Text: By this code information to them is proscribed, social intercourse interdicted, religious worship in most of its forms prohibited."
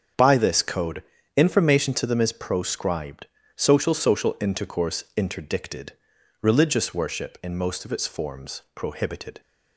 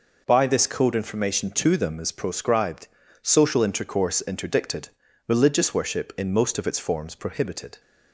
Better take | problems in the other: second | starts louder than the rest; strong; until 1.5 s; 7.5 dB // pauses between "code" and "information"; slight; at 1.0 s; 0.34 s long // says "social" twice; at 3.9 s

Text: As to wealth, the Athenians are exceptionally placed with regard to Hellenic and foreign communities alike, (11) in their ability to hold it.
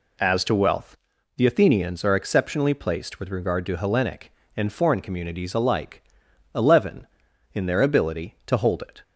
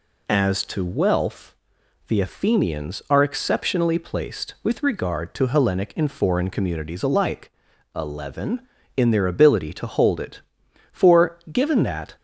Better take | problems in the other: first | goes on to say "For given that"; noticeable; from 10.9 s on; 1.2 s long

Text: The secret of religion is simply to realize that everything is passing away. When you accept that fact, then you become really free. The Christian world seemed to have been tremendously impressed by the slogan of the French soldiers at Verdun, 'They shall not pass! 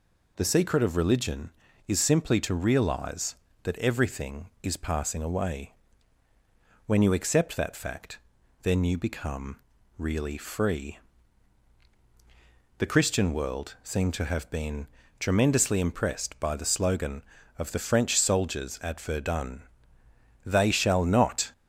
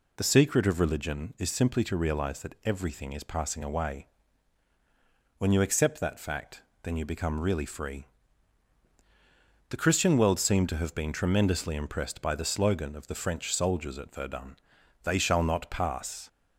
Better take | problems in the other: second | pauses between "become" and "really"; at 9.5 s; 0.40 s long // pauses between "been" and "tremendously"; slight; at 14.8 s; 0.32 s long // stops before "pass"; at 21.5 s

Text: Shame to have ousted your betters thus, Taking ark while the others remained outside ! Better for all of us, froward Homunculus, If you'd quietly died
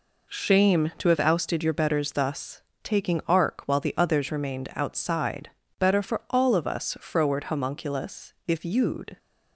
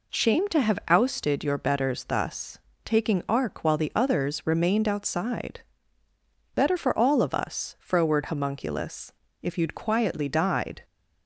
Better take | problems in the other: second | stops before "quietly died"; at 9.1 s

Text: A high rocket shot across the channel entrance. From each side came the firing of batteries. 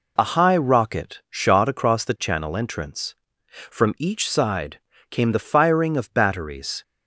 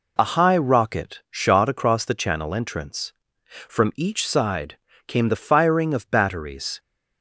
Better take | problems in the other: neither | pauses between "side" and "came"; slight; the same in both

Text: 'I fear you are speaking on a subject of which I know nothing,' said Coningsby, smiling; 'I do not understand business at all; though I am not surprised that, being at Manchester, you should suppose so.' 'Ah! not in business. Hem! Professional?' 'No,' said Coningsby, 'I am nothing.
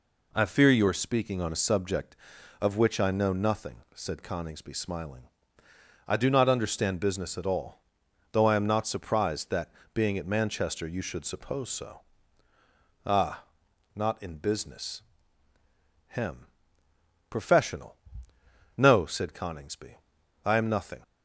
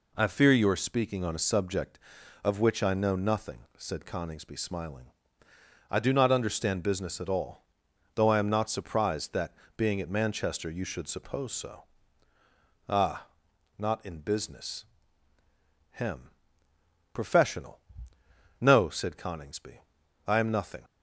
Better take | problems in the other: neither | none

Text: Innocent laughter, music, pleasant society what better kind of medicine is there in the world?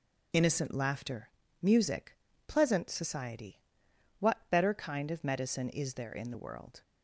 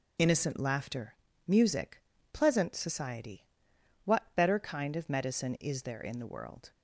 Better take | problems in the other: neither | pauses between "society" and "what"; noticeable; the same in both

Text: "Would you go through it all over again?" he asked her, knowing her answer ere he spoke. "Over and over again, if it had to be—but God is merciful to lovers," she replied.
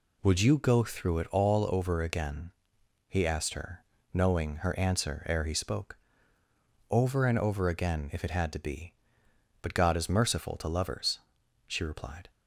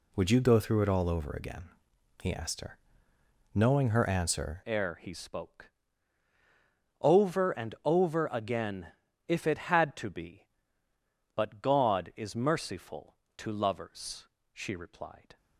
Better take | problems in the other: first | changes voice at "ere"; from 4.6 s on; 10.7 s long

